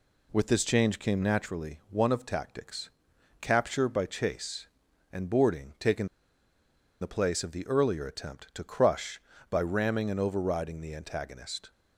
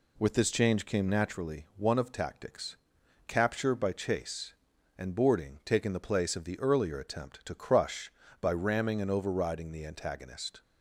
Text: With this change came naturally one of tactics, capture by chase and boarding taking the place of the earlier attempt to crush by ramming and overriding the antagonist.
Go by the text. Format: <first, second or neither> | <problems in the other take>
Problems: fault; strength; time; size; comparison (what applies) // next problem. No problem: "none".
second | pauses between "taking" and "the"; noticeable; at 6.0 s; 0.95 s long